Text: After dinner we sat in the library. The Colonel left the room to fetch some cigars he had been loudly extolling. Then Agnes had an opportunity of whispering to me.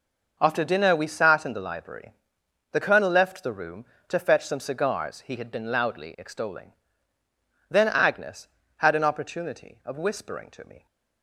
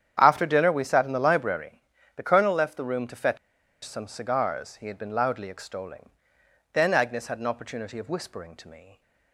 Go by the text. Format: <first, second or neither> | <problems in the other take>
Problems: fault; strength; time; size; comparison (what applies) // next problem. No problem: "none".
first | starts louder than the rest; strong; until 1.2 s; 9 dB // pauses between "fetch" and "some"; noticeable; at 3.3 s; 0.47 s long